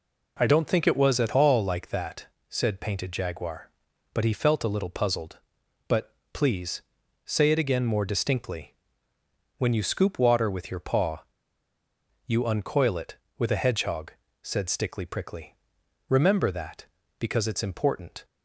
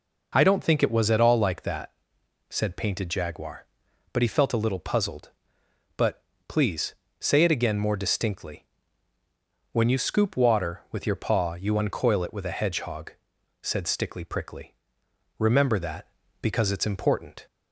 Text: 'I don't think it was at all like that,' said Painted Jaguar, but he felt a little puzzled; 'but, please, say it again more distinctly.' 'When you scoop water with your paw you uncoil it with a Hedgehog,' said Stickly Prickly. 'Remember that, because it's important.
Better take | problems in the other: second | pauses between "paw" and "you"; at 11.2 s; 1.0 s long

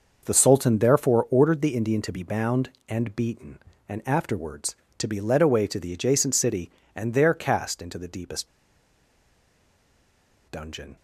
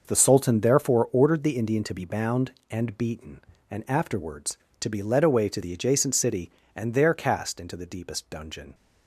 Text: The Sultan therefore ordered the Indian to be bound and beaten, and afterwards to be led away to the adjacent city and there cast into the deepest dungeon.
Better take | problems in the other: second | pauses between "deepest" and "dungeon"; strong; at 8.4 s; 2.0 s long

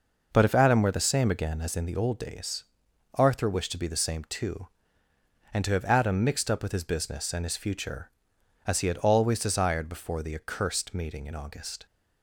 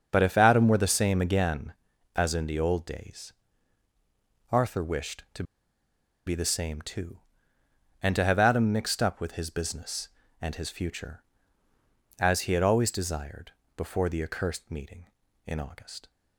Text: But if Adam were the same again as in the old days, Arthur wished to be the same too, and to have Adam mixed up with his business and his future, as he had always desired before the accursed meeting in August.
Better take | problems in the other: first | starts louder than the rest; until 1.1 s; 6.5 dB // pauses between "to" and "be"; noticeable; at 5.4 s; 0.83 s long // pauses between "desired" and "before"; slight; at 13.5 s; 0.24 s long

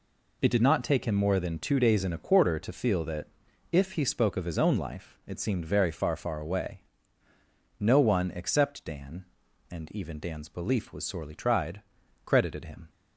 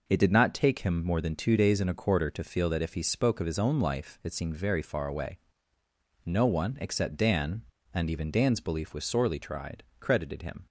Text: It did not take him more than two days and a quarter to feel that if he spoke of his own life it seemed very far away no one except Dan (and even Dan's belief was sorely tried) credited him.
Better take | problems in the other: second | pauses between "that" and "if"; at 3.2 s; 0.44 s long // says "far" twice; at 6.1 s // pauses between "away" and "no"; at 6.7 s; 1.0 s long; noticeable in the second

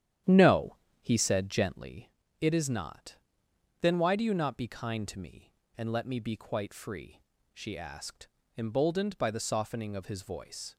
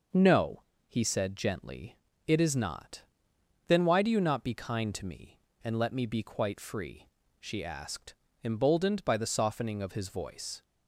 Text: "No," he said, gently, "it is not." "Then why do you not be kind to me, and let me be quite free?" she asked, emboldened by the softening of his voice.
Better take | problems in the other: second | starts louder than the rest; strong; until 1.9 s; 10.5 dB

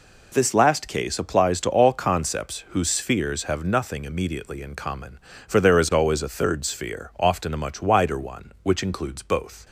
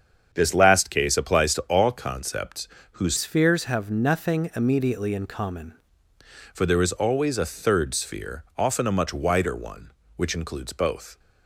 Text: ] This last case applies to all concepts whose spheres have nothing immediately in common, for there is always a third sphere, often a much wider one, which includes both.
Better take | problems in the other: first | starts louder than the rest; strong; until 1.3 s; 7 dB // pauses between "concepts" and "whose"; slight; at 2.6 s; 0.24 s long // changes voice from "spheres" to "common"; from 3.1 to 5.7 s; 2.6 s long

